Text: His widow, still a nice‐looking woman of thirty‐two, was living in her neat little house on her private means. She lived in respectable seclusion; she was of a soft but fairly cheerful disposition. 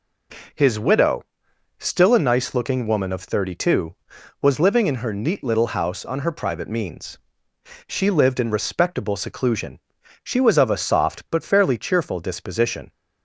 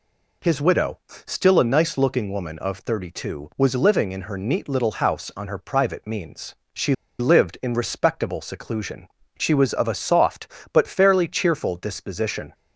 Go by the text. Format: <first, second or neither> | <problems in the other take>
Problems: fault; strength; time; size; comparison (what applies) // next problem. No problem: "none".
first | pauses between "She" and "lived"; slight; at 6.9 s; 0.25 s long